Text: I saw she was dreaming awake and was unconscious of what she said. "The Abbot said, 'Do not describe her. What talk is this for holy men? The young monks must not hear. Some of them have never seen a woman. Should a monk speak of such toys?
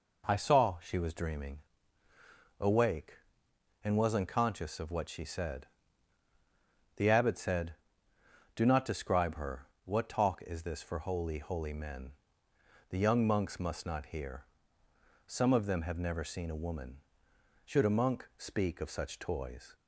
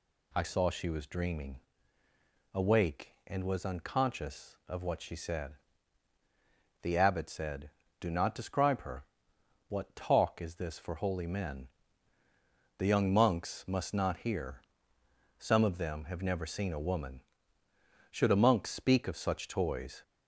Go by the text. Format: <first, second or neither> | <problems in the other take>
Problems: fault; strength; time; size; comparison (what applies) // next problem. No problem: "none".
second | pauses between "dreaming" and "awake"; at 1.5 s; 1.0 s long; noticeable in the second // says "holy" twice; at 11.3 s